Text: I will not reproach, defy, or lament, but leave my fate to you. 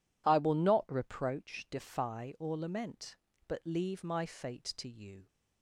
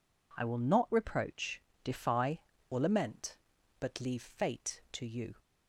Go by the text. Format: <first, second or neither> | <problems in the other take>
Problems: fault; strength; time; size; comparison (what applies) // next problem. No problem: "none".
first | skips "my"; at 4.2 s